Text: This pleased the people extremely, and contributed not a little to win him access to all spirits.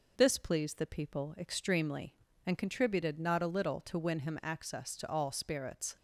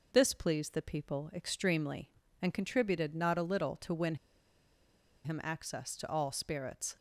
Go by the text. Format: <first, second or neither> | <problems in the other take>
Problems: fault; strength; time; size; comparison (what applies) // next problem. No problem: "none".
first | pauses between "win" and "him"; at 4.1 s; 1.0 s long